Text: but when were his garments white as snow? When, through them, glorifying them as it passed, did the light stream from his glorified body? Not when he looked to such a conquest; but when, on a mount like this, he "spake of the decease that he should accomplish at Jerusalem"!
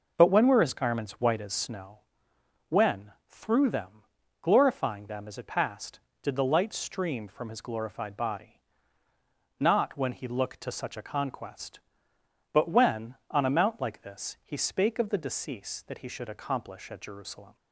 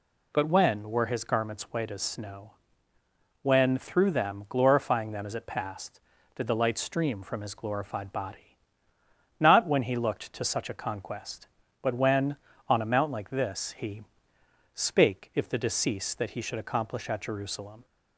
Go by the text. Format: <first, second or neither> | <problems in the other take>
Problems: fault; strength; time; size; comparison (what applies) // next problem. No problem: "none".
first | pauses between "he" and "spake"; noticeable; at 14.0 s; 0.68 s long // says "if" for "of"; at 15.3 s